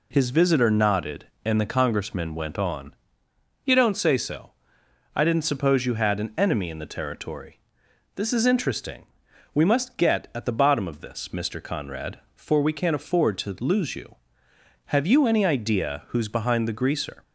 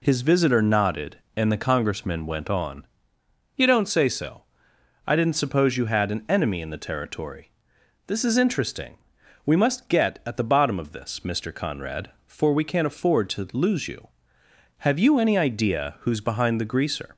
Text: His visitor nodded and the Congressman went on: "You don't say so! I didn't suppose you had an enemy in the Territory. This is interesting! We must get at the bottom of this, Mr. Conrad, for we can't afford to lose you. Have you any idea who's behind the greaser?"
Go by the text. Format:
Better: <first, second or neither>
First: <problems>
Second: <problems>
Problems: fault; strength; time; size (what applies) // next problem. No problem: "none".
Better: neither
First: none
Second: none